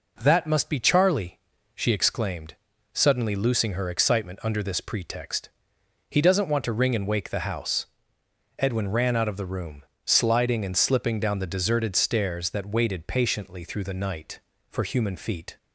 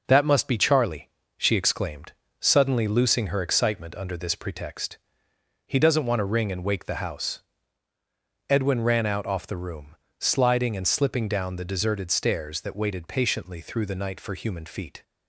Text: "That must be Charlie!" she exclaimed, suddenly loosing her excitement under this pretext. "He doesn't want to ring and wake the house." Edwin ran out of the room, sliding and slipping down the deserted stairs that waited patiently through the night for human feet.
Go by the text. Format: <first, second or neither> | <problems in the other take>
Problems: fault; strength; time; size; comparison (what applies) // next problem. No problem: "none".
first | says "off" for "of"; at 9.2 s